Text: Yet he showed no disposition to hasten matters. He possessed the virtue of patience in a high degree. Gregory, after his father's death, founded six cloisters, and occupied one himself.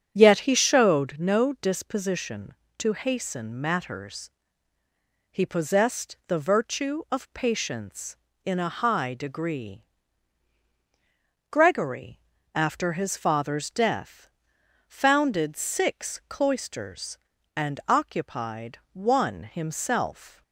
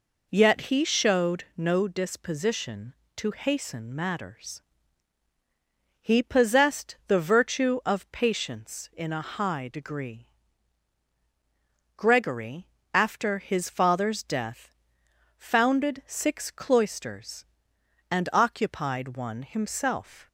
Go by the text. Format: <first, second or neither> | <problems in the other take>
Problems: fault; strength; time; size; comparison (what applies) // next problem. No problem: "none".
second | starts louder than the rest; strong; until 1.2 s; 8 dB // pauses between "occupied" and "one"; slight; at 18.7 s; 0.16 s long